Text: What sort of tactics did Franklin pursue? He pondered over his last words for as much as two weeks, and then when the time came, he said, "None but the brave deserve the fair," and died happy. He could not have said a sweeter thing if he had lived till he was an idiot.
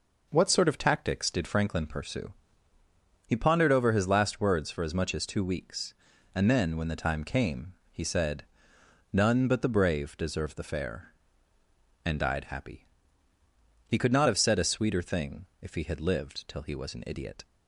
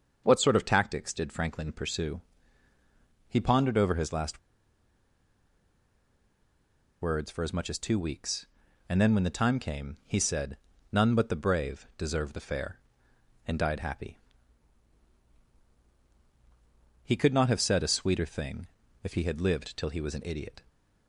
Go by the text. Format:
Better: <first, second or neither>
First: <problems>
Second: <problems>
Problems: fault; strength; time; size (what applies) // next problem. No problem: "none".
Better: first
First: pauses between "thing" and "if"; slight; at 15.4 s; 0.16 s long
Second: starts louder than the rest; until 1.2 s; 6.5 dB // pauses between "last" and "words"; strong; at 4.3 s; 2.6 s long // pauses between "thing" and "if"; slight; at 18.6 s; 0.34 s long